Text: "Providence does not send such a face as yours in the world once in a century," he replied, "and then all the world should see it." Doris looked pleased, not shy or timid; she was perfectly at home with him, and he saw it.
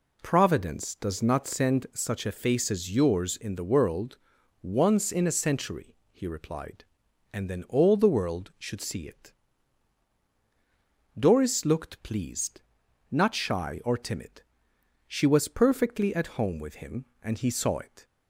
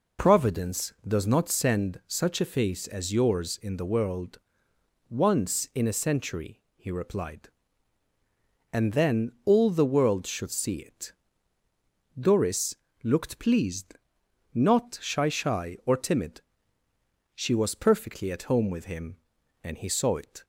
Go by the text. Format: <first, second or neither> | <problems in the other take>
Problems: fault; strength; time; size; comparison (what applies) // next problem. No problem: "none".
first | pauses between "world" and "once"; noticeable; at 4.3 s; 0.70 s long; also in the first // pauses between "Doris" and "looked"; slight; at 12.7 s; 0.26 s long // says "shy" twice; at 15.2 s